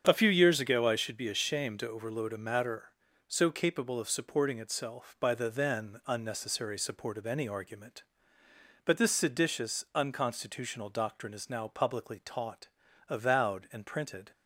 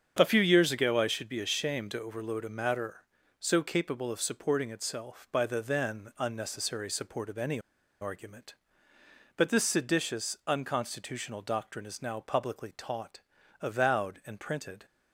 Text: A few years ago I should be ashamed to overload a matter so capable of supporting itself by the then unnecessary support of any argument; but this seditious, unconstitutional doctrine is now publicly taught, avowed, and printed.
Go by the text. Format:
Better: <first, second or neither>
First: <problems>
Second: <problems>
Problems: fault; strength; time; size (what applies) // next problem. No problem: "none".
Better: first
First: starts louder than the rest; strong; until 1.0 s; 8 dB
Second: starts louder than the rest; strong; until 1.2 s; 7.5 dB // pauses between "any" and "argument"; at 7.5 s; 0.41 s long